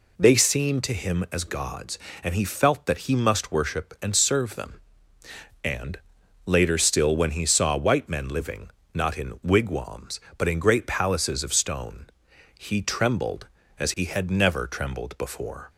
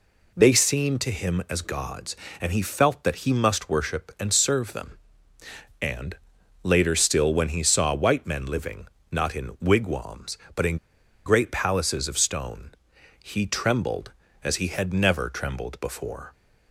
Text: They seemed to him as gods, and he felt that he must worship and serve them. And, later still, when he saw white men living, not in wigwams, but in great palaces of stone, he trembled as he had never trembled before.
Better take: first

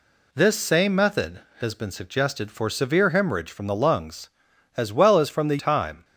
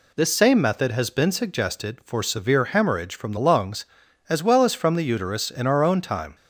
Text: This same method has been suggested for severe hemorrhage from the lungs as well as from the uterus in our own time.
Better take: second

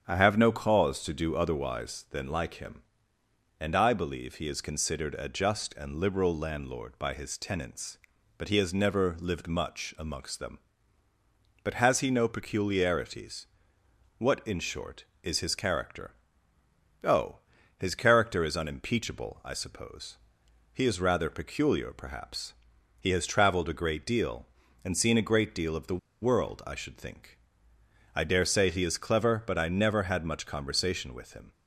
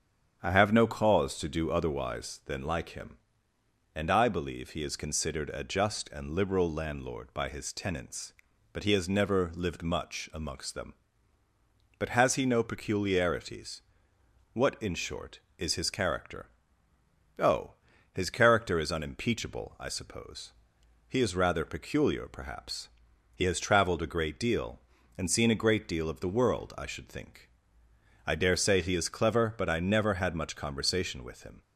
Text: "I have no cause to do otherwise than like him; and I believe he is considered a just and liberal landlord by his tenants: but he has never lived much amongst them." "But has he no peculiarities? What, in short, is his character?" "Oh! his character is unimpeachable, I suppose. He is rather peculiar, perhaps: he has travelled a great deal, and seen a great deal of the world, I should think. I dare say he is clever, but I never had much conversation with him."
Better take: second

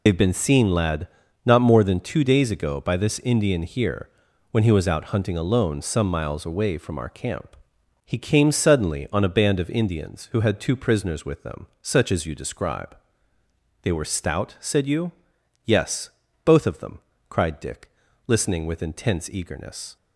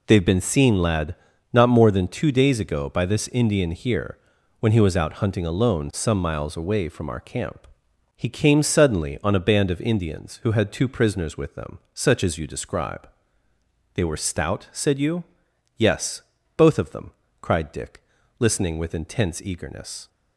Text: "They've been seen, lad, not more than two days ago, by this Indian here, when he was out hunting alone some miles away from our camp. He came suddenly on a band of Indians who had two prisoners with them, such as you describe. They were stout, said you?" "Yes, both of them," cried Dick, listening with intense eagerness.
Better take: second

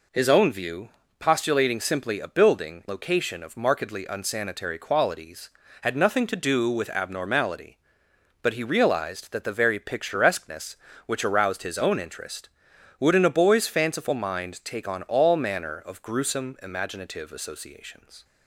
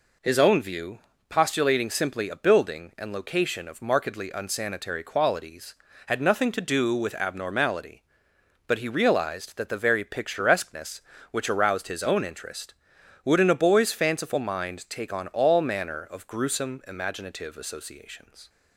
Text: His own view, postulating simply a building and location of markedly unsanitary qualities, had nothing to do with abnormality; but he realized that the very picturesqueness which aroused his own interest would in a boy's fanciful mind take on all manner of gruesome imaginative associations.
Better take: second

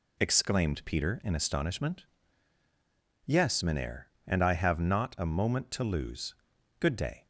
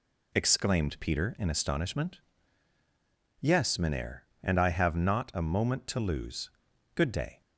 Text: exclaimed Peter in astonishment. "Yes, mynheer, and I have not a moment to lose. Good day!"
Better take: neither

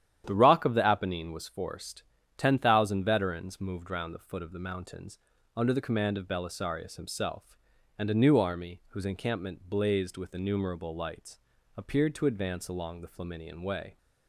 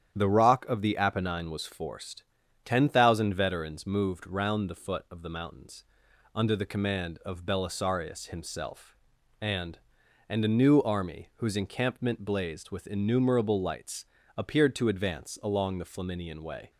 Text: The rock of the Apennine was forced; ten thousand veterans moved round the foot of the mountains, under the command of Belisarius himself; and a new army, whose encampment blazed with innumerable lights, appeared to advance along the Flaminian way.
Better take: first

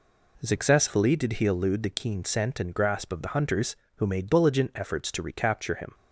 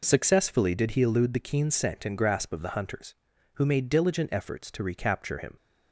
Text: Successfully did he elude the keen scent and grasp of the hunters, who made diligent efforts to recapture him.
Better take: neither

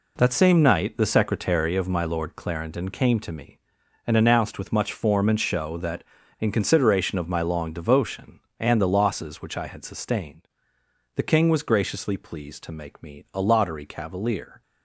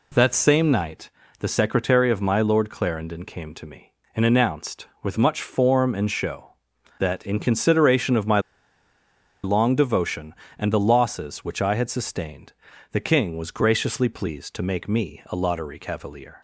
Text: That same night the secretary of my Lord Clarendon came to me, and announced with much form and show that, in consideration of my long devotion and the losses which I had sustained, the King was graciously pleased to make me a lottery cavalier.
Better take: first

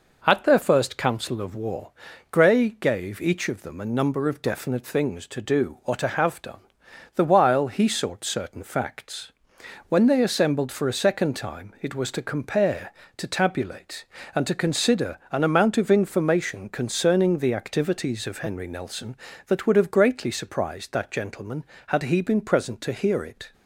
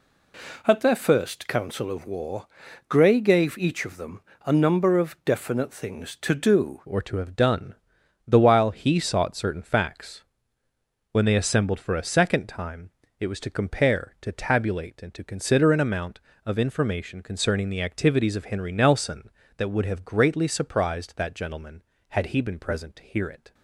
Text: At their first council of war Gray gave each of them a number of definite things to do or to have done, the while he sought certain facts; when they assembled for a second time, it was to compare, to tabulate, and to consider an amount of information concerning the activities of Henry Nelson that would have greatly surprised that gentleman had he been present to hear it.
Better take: first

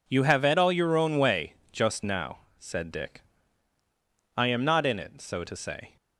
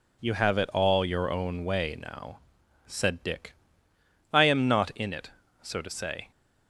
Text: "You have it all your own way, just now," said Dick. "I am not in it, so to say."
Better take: first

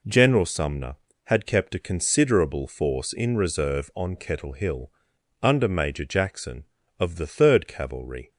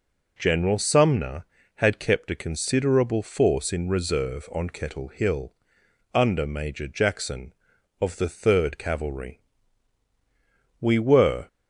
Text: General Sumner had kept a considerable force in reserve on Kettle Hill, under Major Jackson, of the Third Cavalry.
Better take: first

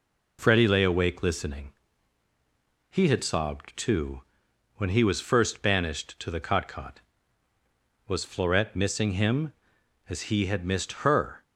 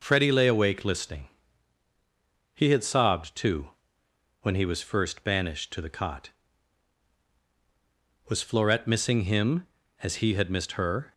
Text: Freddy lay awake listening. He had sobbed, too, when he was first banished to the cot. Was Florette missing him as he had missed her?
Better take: second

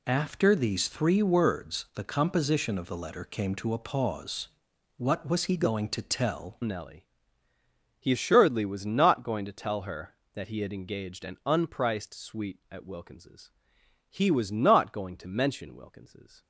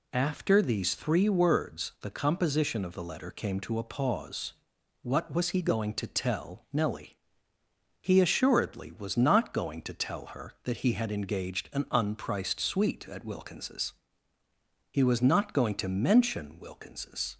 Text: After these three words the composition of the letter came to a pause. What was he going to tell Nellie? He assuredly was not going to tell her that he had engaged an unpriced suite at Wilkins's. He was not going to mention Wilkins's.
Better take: second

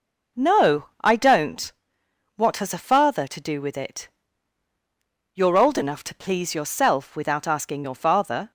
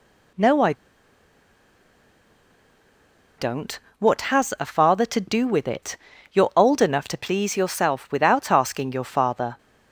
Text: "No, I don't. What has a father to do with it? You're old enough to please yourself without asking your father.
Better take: first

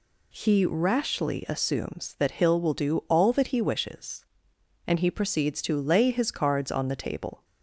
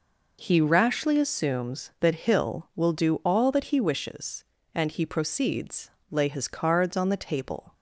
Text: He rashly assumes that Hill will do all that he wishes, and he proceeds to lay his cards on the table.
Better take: first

